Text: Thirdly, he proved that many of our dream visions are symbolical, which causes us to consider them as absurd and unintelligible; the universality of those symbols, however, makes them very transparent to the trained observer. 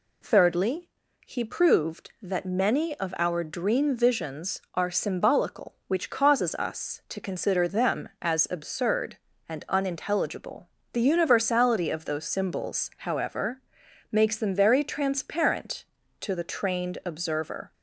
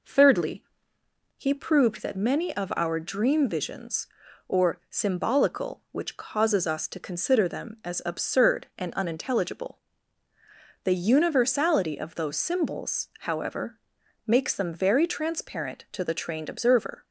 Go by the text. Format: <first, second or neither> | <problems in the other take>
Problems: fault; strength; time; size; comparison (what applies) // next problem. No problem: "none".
first | says "or" for "are"; at 4.4 s